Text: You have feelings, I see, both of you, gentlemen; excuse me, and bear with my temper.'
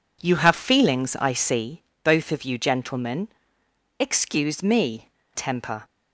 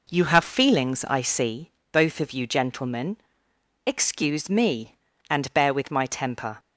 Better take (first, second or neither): second